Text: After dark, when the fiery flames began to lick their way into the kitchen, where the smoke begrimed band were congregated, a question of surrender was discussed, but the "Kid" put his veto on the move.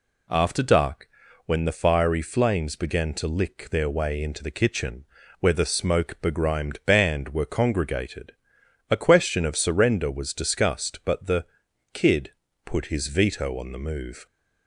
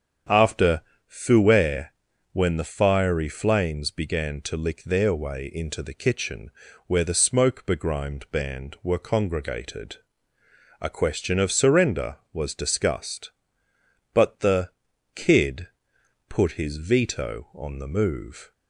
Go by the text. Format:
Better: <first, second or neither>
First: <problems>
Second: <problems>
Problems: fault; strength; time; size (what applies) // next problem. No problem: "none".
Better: first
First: pauses between "the" and "Kid"; noticeable; at 11.4 s; 0.48 s long // pauses between "Kid" and "put"; slight; at 12.3 s; 0.34 s long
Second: starts louder than the rest; strong; until 1.5 s; 7.5 dB // says "fouet" for "dark"; at 1.0 s // pauses between "the" and "Kid"; noticeable; at 14.6 s; 0.46 s long // pauses between "Kid" and "put"; noticeable; at 15.6 s; 0.62 s long